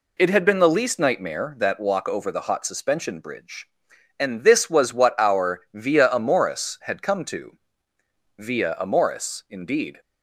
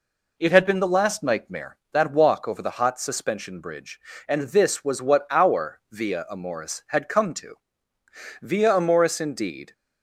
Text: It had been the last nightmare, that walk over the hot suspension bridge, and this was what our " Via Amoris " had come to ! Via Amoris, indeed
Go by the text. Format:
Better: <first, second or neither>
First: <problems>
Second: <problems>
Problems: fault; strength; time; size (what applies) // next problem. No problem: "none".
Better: second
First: says "least" for "last"; at 0.6 s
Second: none